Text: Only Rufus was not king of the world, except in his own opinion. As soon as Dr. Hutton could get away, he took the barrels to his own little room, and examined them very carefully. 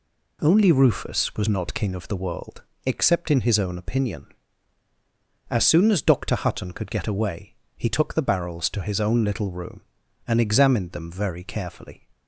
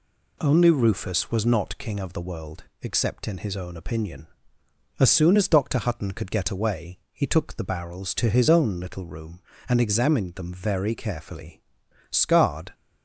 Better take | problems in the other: first | goes on to say "Scarred"; noticeable; from 12.0 s on; 0.64 s long

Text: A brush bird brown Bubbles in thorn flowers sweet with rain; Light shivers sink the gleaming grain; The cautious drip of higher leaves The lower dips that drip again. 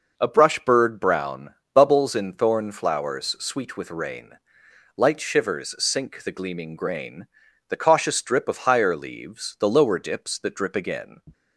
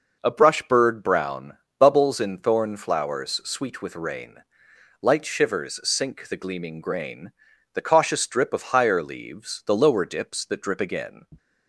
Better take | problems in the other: neither | pauses between "brown" and "Bubbles"; slight; the same in both

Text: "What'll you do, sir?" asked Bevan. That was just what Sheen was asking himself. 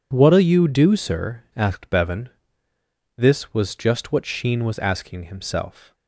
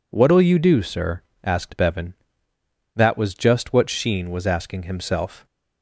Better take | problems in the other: second | says "This" for "That"; at 3.1 s

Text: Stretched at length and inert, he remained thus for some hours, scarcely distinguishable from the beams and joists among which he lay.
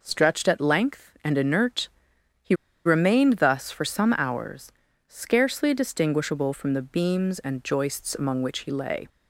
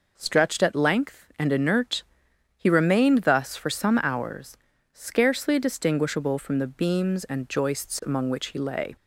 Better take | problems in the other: second | pauses between "he" and "remained"; slight; at 2.5 s; 0.30 s long

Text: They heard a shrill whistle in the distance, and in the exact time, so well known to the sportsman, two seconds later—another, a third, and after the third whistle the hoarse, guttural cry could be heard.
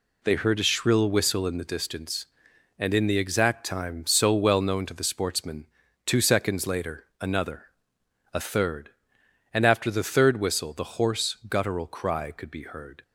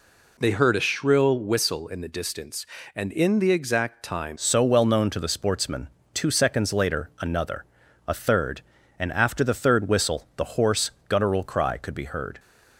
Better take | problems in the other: first | changes voice at "so"; from 4.3 s on; 8.0 s long

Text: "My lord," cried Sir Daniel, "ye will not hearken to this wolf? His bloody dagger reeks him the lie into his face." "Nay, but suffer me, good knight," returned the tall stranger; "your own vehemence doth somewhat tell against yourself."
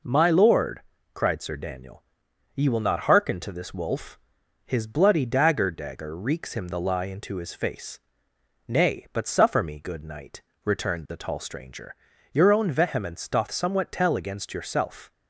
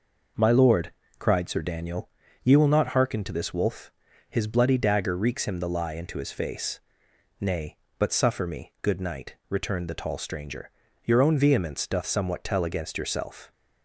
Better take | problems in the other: second | says "dagger" twice; at 5.7 s

